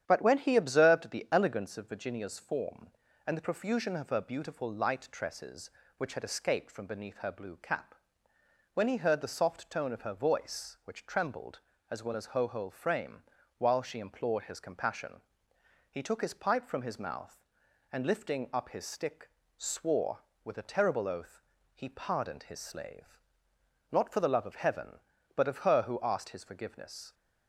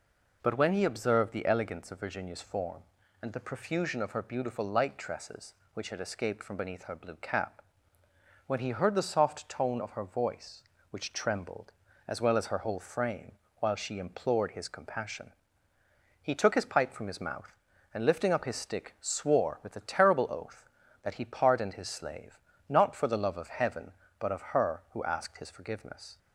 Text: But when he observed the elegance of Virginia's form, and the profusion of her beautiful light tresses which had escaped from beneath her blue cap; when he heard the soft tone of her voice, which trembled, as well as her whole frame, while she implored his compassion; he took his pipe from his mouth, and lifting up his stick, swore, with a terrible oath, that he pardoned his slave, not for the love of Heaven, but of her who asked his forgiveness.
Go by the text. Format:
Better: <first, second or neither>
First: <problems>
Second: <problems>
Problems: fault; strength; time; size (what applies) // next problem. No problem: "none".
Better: second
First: starts louder than the rest; strong; until 1.0 s; 9.5 dB // skips "that"; at 21.5 s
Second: none